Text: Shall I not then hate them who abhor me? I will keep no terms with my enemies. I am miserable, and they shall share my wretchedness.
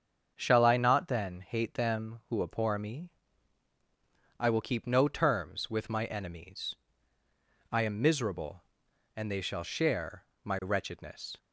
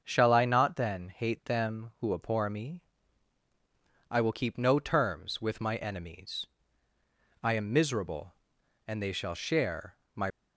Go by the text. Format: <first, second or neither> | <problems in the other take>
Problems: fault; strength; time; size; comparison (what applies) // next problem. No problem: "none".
first | starts louder than the rest; until 1.0 s; 7 dB; strong in the first // pauses between "share" and "my"; slight; at 9.9 s; 0.18 s long; slight in the first // stops before "wretchedness"; at 10.2 s